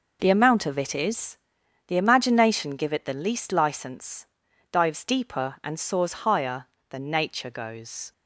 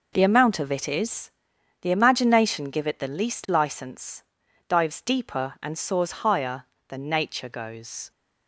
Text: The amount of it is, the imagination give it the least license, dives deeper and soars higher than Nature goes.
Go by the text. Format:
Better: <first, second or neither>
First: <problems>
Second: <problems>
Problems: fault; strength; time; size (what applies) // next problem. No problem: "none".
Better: neither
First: none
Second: none